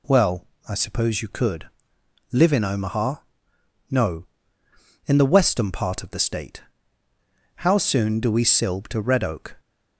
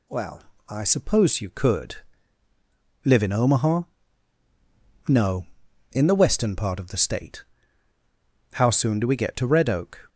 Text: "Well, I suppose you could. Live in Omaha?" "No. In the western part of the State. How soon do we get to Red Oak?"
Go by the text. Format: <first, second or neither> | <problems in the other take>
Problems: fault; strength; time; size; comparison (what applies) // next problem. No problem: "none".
second | says "silb" for "get"; at 8.4 s